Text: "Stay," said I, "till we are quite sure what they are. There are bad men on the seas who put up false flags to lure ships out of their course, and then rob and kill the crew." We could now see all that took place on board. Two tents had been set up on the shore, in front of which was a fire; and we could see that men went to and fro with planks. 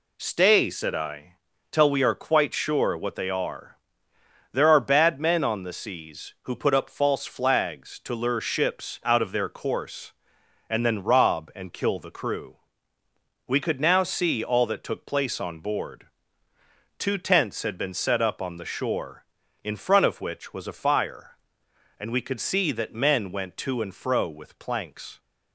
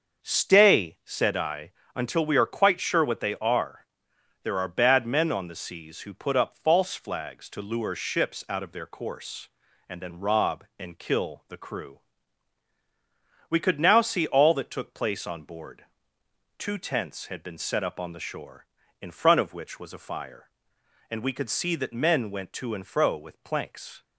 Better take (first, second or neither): first